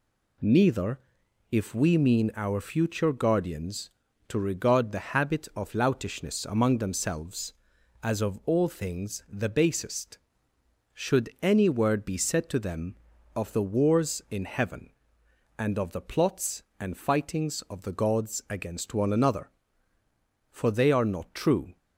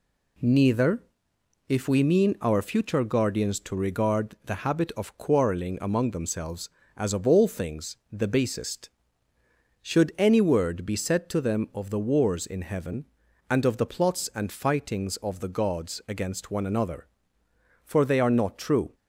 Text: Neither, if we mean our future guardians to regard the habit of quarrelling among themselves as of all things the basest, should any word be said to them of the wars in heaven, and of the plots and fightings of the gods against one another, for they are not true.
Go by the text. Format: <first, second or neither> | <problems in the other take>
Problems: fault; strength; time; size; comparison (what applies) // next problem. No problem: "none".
second | says "loutishness" for "quarrelling"; at 5.7 s